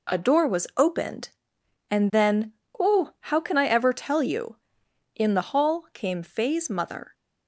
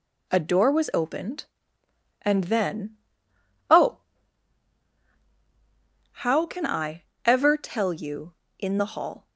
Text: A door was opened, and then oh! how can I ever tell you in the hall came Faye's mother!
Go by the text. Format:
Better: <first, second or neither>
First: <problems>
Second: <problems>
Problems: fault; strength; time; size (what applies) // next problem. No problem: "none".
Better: first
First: pauses between "then" and "oh"; slight; at 2.5 s; 0.26 s long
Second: pauses between "then" and "oh"; noticeable; at 2.9 s; 0.72 s long // pauses between "I" and "ever"; slight; at 7.0 s; 0.20 s long // stops before "came Faye's mother"; at 9.2 s